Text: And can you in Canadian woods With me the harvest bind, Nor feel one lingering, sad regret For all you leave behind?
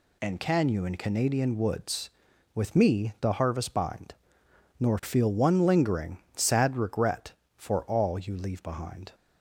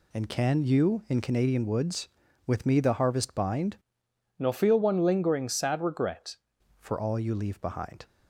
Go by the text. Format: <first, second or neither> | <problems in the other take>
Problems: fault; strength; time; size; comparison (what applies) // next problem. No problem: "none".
first | changes voice from "Nor" to "regret"; from 4.3 to 6.3 s; 2.0 s long